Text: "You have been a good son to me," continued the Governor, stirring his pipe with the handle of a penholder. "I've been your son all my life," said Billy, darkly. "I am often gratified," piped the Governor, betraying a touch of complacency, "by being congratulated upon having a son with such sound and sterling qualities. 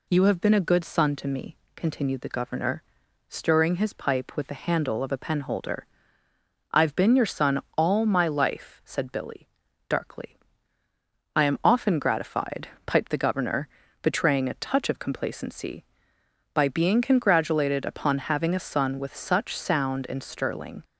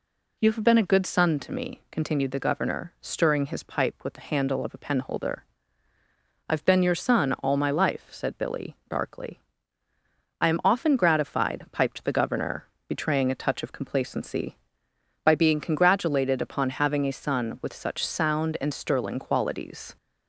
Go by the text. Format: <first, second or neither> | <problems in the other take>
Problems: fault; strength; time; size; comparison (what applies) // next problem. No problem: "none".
second | pauses between "son" and "all"; slight; at 7.5 s; 0.16 s long // stops before "qualities"; at 20.8 s